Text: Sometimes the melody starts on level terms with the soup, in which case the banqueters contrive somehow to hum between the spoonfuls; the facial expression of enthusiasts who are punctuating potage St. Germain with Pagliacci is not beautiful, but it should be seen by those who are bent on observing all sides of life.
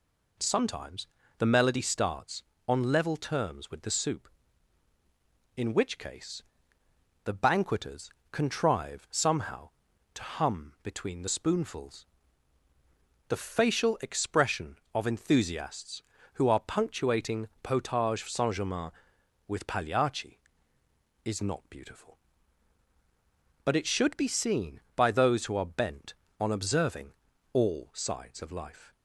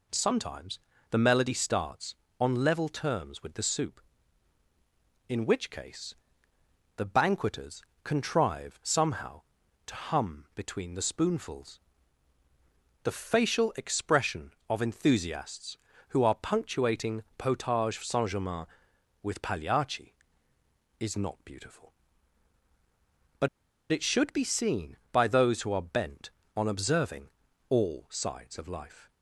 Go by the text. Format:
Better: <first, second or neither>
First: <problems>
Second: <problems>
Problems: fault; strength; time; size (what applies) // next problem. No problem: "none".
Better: first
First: pauses between "Sometimes" and "the"; slight; at 1.0 s; 0.30 s long // pauses between "case" and "the"; noticeable; at 6.4 s; 0.82 s long // pauses between "banqueters" and "contrive"; slight; at 8.0 s; 0.22 s long // pauses between "observing" and "all"; at 27.1 s; 0.40 s long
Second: pauses between "Sometimes" and "the"; slight; at 0.7 s; 0.30 s long // pauses between "case" and "the"; noticeable; at 6.1 s; 0.82 s long // pauses between "banqueters" and "contrive"; slight; at 7.8 s; 0.22 s long // pauses between "but" and "it"; at 23.4 s; 0.44 s long // pauses between "observing" and "all"; at 27.2 s; 0.40 s long